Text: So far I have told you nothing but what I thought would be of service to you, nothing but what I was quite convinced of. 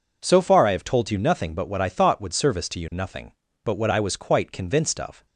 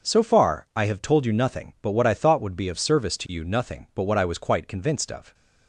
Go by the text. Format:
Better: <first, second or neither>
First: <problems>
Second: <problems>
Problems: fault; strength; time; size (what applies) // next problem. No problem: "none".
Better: second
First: skips "be of"; at 2.3 s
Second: none